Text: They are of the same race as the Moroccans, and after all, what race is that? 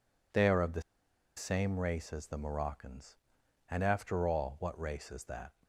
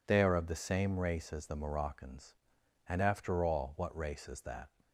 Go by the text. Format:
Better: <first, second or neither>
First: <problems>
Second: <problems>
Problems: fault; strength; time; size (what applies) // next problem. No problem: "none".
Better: second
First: pauses between "the" and "same"; noticeable; at 0.8 s; 0.54 s long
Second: none